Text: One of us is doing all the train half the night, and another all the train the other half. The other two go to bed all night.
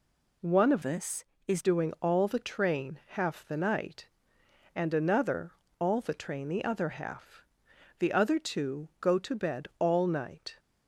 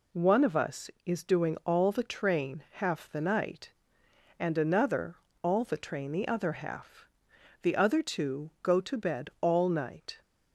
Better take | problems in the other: second | changes voice from "us" to "is"; from 0.8 to 1.6 s; 0.8 s long // pauses between "another" and "all"; slight; at 5.5 s; 0.26 s long; slight in the second

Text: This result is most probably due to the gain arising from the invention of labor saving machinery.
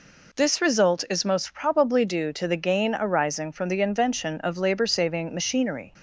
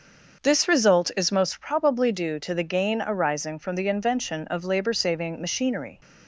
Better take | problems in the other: first | starts louder than the rest; until 1.7 s; 6.5 dB

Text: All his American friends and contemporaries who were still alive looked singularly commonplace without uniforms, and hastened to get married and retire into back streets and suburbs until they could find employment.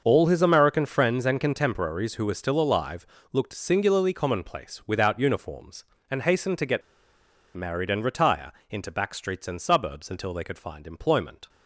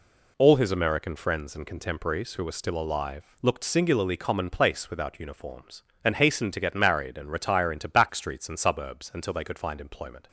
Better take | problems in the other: second | starts louder than the rest; until 1.0 s; 6.5 dB // pauses between "alive" and "looked"; slight; at 3.0 s; 0.26 s long // pauses between "get" and "married"; noticeable; at 6.8 s; 0.75 s long // pauses between "retire" and "into"; slight; at 8.5 s; 0.16 s long

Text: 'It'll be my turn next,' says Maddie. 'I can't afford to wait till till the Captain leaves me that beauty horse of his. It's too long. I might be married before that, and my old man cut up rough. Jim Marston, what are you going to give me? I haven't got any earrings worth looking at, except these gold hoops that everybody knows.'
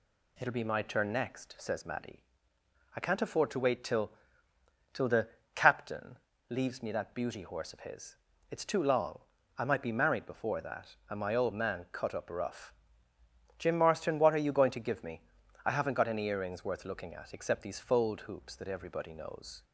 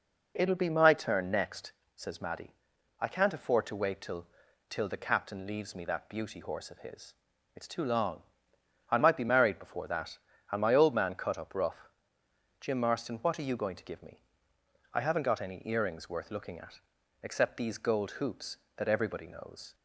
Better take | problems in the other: second | pauses between "till" and "till"; noticeable; at 4.1 s; 0.80 s long; also in the second // pauses between "the" and "Captain"; slight; at 5.2 s; 0.26 s long // pauses between "Captain" and "leaves"; slight; at 6.1 s; 0.32 s long // says "fold" for "gold"; at 17.7 s

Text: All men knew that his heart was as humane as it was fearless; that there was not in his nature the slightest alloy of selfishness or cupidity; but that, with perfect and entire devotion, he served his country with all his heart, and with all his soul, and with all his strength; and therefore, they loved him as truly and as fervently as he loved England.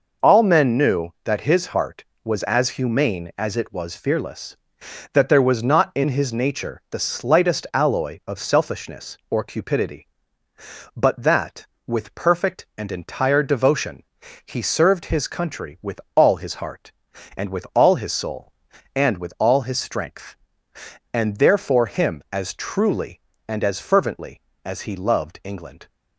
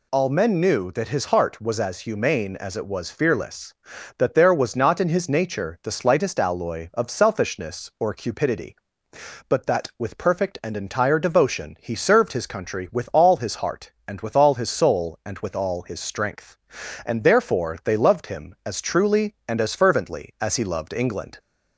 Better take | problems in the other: second | skips "they loved"; at 21.8 s

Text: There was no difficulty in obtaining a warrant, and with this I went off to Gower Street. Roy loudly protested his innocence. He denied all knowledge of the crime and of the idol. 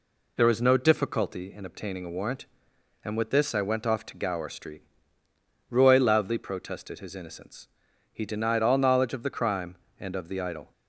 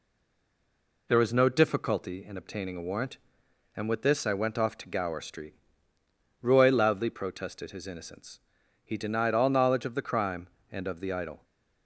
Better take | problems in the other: first | stays silent before the first word; until 1.0 s; 1.0 s long

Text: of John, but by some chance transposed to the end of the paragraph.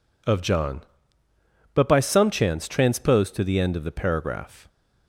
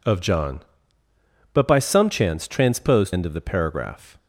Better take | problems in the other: first | skips "to the"; at 3.1 s

